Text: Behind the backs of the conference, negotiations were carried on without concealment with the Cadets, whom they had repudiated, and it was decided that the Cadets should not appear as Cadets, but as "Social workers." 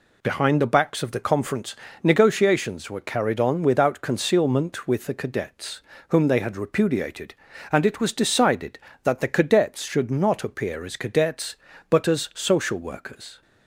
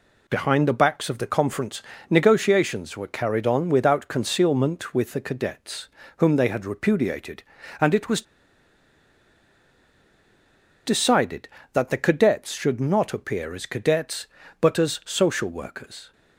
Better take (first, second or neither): first